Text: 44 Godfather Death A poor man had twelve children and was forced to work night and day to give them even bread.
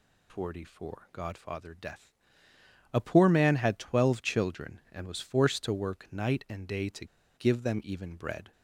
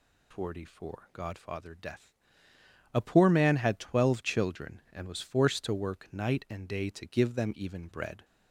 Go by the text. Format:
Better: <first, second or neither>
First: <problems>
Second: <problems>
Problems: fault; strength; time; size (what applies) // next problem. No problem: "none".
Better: second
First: pauses between "Death" and "A"; noticeable; at 2.1 s; 0.80 s long // pauses between "to" and "give"; slight; at 7.0 s; 0.31 s long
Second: pauses between "Death" and "A"; noticeable; at 2.1 s; 0.80 s long